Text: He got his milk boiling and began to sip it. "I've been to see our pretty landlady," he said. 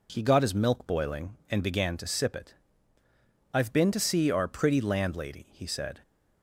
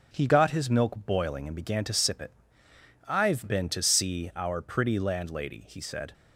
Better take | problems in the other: first | gets quieter; noticeable; throughout; 4.5 dB

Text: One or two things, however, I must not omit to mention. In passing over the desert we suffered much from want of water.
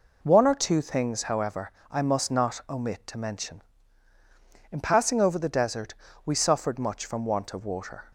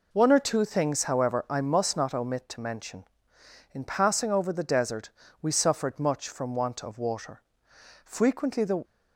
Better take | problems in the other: first | pauses between "desert" and "we"; slight; at 5.0 s; 0.30 s long; slight in the first // goes on to say "Frequently the"; noticeable; from 8.0 s on; 0.80 s long

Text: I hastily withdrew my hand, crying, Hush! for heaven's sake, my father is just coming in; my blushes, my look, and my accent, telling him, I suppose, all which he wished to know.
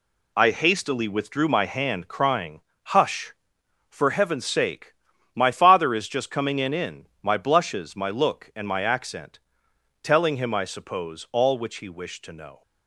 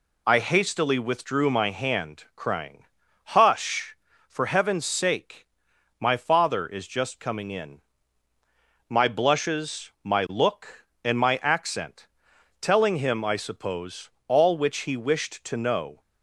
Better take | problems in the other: second | says "in" twice; at 6.7 s

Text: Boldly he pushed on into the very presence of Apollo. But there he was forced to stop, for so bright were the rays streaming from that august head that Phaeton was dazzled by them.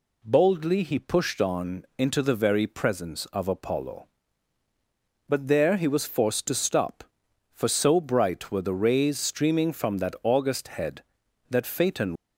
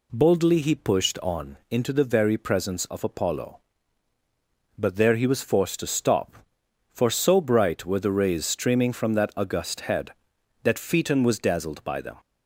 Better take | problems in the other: second | stops before "was dazzled by them"; at 12.1 s

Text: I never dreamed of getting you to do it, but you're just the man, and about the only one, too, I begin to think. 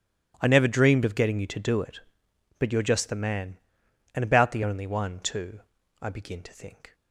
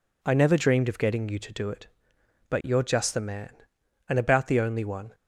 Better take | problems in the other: first | stops before "too I begin to think"; at 5.1 s

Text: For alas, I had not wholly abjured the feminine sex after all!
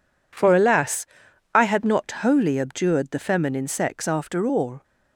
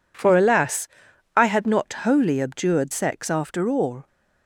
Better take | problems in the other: first | skips "the feminine"; at 2.9 s

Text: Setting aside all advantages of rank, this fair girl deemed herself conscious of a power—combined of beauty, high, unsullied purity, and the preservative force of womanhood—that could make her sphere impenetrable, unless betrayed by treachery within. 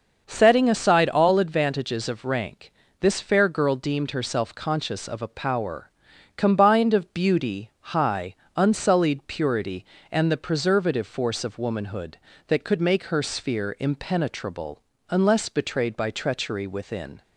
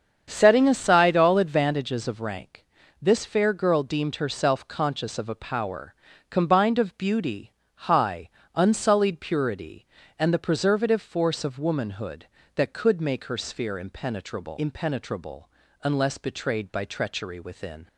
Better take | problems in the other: first | starts louder than the rest; strong; until 1.3 s; 7.5 dB; noticeable in the first // says "impenetrable" twice; at 14.5 s

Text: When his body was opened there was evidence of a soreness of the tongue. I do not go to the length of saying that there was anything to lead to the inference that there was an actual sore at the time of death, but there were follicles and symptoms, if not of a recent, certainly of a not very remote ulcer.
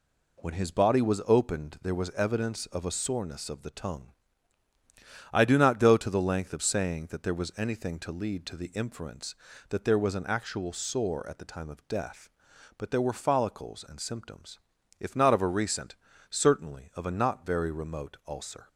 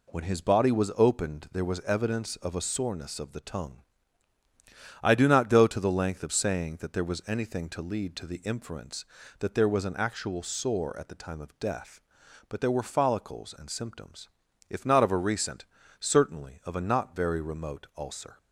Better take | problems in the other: neither | none

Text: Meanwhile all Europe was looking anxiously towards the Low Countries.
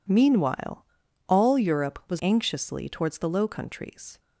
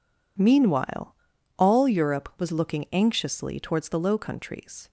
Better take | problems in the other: second | pauses between "Meanwhile" and "all"; at 0.8 s; 0.42 s long; also in the second // skips "looking"; at 2.2 s

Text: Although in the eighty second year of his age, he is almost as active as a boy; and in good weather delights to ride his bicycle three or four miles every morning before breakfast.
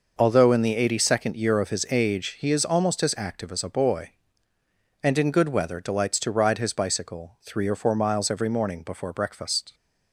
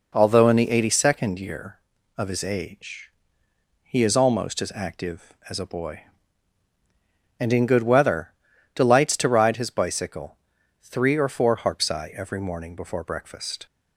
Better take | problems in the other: first | pauses between "weather" and "delights"; at 8.3 s; 0.44 s long // pauses between "bicycle" and "three"; noticeable; at 10.3 s; 0.46 s long // says "harpsi" for "miles"; at 11.5 s

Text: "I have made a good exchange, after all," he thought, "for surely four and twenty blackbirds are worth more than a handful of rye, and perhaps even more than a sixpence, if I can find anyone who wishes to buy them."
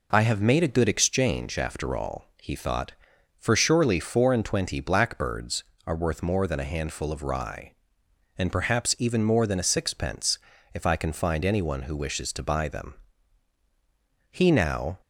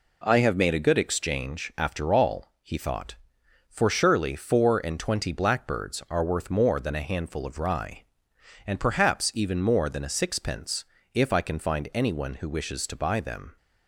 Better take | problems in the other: second | goes on to say "He now"; noticeable; from 14.3 s on; 0.68 s long

